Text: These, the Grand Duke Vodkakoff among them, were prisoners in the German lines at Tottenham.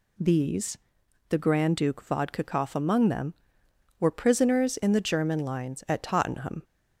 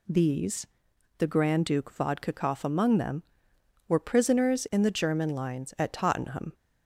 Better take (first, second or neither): neither